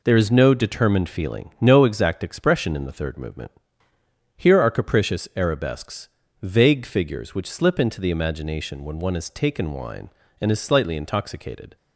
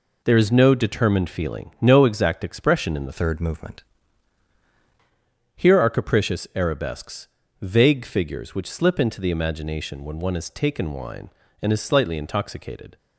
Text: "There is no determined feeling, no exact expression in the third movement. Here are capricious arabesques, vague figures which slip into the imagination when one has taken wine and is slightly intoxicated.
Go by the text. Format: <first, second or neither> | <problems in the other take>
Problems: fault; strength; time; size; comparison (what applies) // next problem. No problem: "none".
first | changes voice from "third" to "movement"; from 3.1 to 3.8 s; 0.7 s long